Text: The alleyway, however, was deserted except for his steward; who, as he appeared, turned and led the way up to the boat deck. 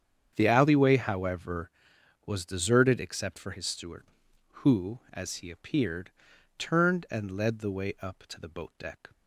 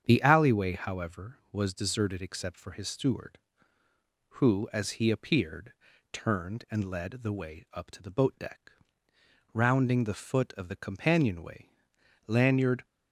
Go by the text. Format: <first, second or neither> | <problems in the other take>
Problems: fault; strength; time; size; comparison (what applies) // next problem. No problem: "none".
first | starts louder than the rest; strong; until 1.0 s; 8 dB; strong in the first // goes on to say "Rounding the foot of the companionway Lanyard"; strong; from 9.5 s on; 3.3 s long